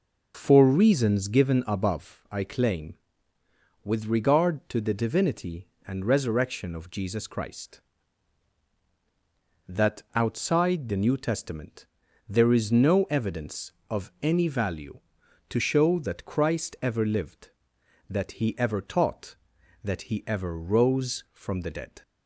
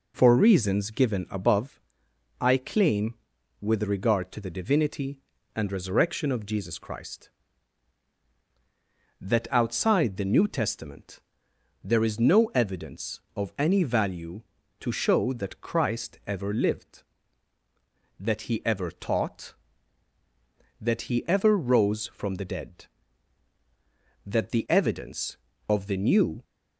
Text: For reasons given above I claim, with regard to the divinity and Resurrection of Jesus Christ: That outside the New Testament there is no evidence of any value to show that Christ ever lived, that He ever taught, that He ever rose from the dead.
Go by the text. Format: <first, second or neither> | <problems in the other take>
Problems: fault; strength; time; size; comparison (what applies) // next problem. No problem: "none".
first | pauses between "above" and "I"; noticeable; at 1.8 s; 0.58 s long // pauses between "Testament" and "there"; noticeable; at 11.1 s; 0.64 s long; also in the first // goes on to say "That the evidence of the New"; strong; from 24.2 s on; 2.1 s long